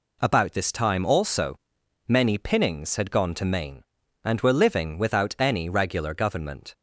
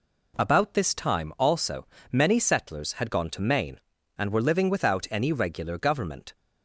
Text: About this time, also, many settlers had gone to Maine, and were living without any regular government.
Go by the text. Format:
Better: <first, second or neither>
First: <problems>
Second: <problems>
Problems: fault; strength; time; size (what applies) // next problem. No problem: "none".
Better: second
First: says "pinnings" for "settlers"; at 2.3 s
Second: none